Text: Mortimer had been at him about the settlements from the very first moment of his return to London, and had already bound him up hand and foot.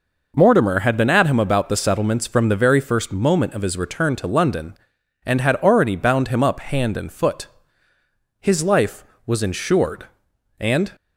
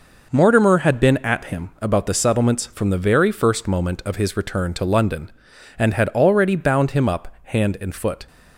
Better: second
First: goes on to say "His life was insured and"; strong; from 8.4 s on; 2.5 s long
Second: none

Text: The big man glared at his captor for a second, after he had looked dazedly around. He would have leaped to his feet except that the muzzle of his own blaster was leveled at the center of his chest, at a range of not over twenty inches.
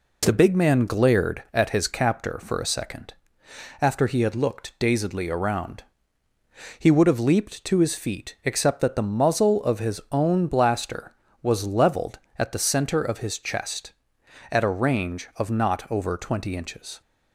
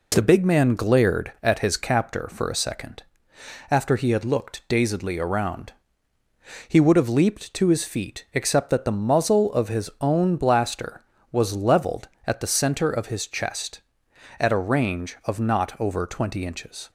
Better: neither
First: none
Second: none

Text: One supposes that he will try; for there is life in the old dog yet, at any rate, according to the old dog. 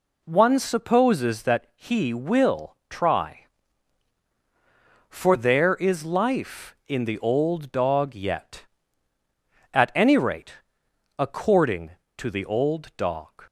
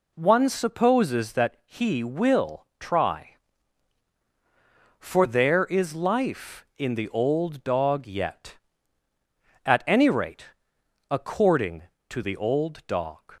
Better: neither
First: none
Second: none

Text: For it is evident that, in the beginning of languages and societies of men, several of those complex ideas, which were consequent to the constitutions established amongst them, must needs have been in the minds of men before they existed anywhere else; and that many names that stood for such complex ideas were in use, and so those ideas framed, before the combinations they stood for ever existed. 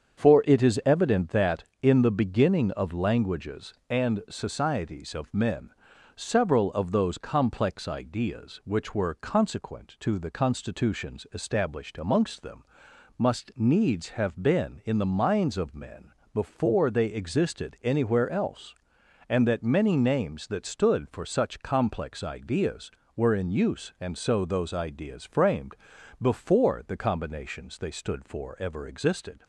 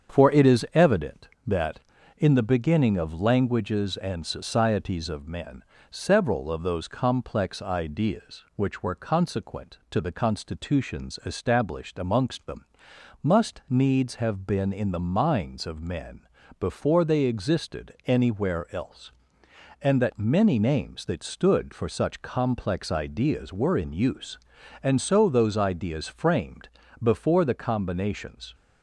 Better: first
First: starts louder than the rest; strong; until 1.2 s; 7.5 dB // pauses between "men" and "before"; slight; at 16.1 s; 0.24 s long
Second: starts louder than the rest; strong; until 1.2 s; 7.5 dB // pauses between "men" and "before"; slight; at 16.2 s; 0.36 s long // stops before "they stood for ever existed"; at 28.5 s

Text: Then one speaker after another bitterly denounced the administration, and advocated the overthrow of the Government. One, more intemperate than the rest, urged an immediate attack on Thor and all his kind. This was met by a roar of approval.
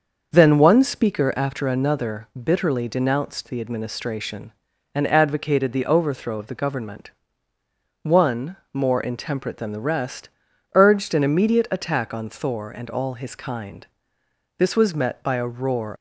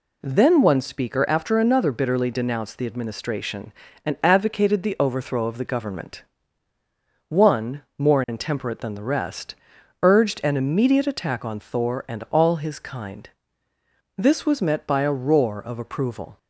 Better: second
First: starts louder than the rest; until 1.3 s; 6.5 dB // stops before "of approval"; at 15.9 s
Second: none

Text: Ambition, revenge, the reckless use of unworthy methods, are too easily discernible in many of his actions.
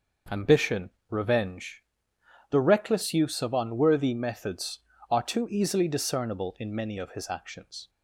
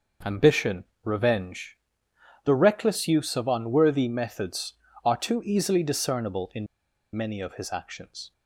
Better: first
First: none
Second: pauses between "in" and "many"; noticeable; at 6.6 s; 0.49 s long

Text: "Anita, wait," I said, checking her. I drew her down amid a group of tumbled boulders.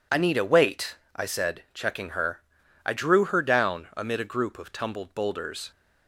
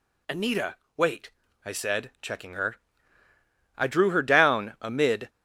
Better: first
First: none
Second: stops before "a group of tumbled boulders"; at 5.2 s

